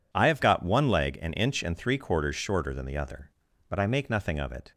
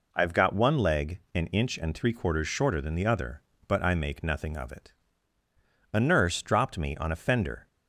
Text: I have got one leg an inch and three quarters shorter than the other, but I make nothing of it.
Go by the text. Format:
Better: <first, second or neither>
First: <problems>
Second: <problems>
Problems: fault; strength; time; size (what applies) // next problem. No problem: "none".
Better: first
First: none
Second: goes on to say "A nurse dropped me on a fender"; strong; from 5.9 s on; 1.7 s long